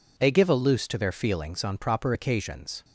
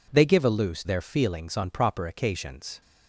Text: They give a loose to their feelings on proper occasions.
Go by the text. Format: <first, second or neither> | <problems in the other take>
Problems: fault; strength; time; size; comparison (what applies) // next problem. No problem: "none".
first | skips "to"; at 0.8 s